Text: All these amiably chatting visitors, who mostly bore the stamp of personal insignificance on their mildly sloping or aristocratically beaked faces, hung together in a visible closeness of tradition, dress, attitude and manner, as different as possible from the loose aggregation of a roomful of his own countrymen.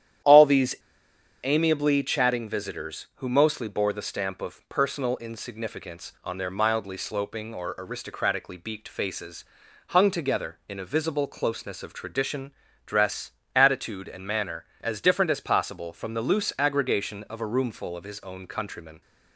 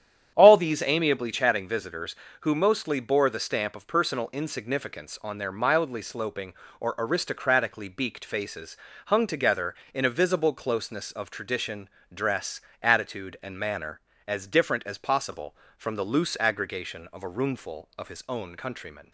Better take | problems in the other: second | starts louder than the rest; strong; until 1.9 s; 10.5 dB; strong in the second // pauses between "these" and "amiably"; noticeable; at 0.7 s; 0.66 s long

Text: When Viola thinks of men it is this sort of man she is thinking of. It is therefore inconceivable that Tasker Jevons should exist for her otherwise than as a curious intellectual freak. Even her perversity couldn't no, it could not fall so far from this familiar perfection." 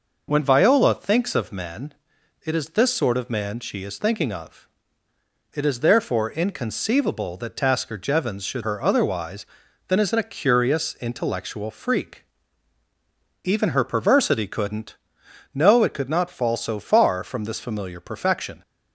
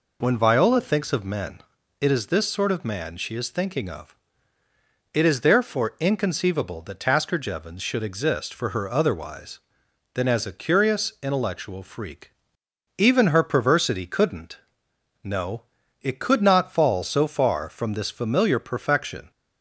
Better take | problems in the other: second | pauses between "men" and "it"; noticeable; at 1.9 s; 0.54 s long; also in the second // skips "exist for"; at 8.6 s // pauses between "couldn't" and "no"; noticeable; at 14.9 s; 0.60 s long; noticeable in the second

